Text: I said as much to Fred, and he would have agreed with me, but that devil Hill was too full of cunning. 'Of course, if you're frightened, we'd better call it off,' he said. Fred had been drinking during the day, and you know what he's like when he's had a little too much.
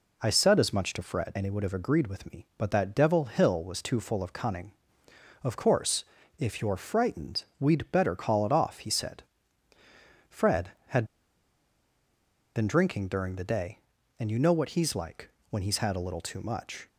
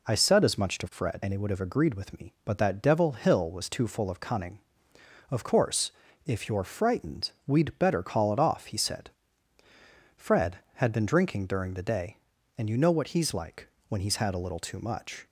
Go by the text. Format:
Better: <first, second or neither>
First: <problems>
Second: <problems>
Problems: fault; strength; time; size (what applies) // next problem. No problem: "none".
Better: second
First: pauses between "had" and "been"; strong; at 11.0 s; 1.5 s long // pauses between "like" and "when"; slight; at 15.2 s; 0.22 s long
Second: pauses between "like" and "when"; slight; at 13.6 s; 0.22 s long